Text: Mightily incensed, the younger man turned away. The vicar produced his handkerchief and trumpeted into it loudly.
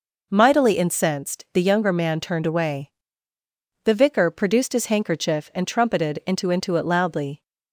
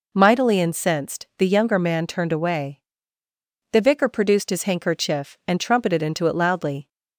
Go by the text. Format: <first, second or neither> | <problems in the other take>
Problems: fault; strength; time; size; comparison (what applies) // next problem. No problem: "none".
second | says "into" twice; at 6.5 s